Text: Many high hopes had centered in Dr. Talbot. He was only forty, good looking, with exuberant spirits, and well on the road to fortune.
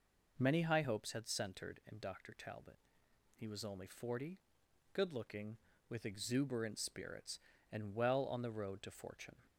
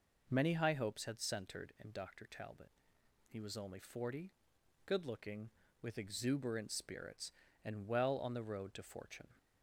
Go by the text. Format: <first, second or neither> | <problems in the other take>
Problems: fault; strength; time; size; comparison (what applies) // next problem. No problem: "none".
neither | none